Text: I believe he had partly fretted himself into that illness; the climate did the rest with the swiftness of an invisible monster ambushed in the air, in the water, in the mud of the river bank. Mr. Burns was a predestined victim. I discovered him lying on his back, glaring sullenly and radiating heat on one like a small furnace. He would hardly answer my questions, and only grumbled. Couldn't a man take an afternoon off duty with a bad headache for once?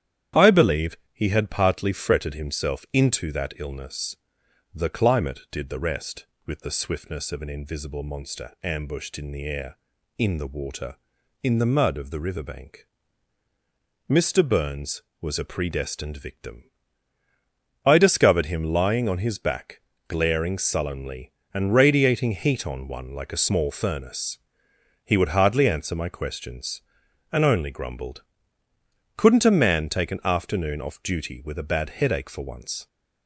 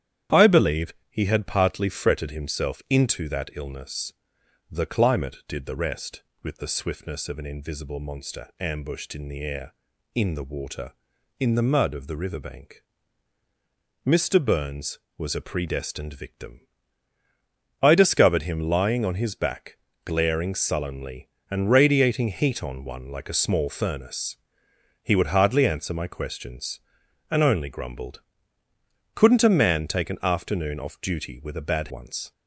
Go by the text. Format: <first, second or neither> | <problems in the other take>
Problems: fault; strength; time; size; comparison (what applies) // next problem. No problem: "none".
first | starts louder than the rest; strong; until 1.4 s; 10 dB; strong in the first // pauses between "believe" and "he"; slight; at 0.9 s; 0.16 s long; slight in the first // skips "headache for"; at 31.8 s